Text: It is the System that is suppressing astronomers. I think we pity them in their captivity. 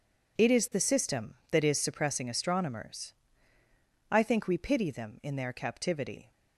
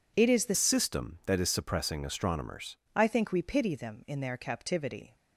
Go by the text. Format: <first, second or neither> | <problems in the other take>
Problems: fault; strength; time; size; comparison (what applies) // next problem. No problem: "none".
first | changes voice from "System" to "astronomers"; from 0.5 to 2.7 s; 2.2 s long